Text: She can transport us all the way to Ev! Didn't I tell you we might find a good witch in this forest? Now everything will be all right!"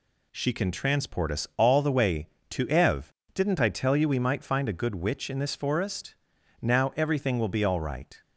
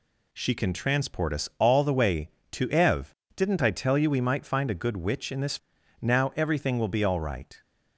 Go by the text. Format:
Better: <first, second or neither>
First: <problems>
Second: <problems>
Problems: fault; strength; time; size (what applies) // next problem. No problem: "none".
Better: first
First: none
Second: skips "forest"; at 5.7 s